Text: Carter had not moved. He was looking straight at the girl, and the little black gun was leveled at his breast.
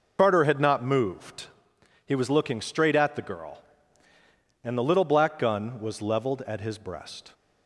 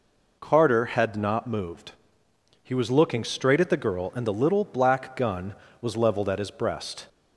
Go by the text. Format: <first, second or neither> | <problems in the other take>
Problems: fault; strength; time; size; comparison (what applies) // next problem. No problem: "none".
second | loses the start of "Carter"; at 0.1 s; 60 ms